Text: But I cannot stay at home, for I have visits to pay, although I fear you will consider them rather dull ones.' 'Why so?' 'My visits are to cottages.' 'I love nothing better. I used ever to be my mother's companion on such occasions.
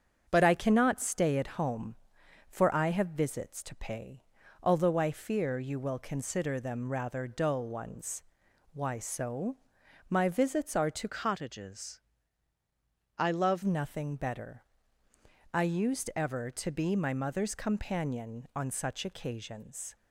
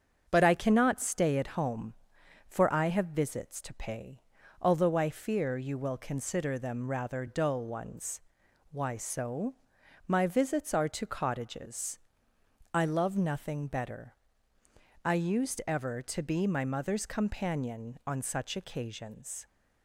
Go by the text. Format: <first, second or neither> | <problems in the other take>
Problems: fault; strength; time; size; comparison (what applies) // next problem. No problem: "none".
second | starts louder than the rest; strong; until 1.3 s; 7 dB; strong in the second // changes voice from "cottages" to "love"; from 11.0 to 13.6 s; 2.6 s long